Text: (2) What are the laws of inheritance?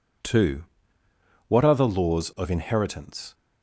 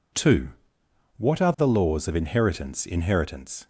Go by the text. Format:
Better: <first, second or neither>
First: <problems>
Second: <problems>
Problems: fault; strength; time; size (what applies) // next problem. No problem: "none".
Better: first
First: none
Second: says "inheritance" twice; at 2.8 s